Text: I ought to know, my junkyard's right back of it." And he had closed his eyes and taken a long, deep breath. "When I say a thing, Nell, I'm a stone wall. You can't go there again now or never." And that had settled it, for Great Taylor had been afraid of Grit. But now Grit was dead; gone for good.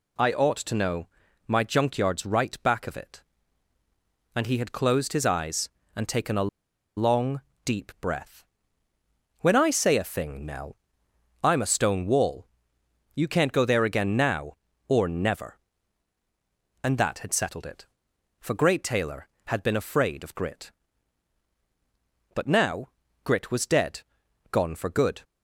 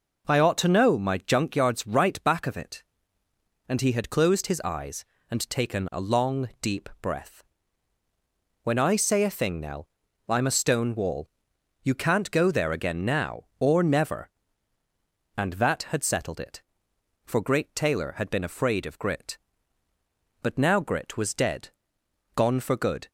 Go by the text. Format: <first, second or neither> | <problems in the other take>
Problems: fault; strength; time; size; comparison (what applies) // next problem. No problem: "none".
second | pauses between "a" and "long"; noticeable; at 6.4 s; 0.48 s long // pauses between "now" and "Grit"; at 22.8 s; 0.38 s long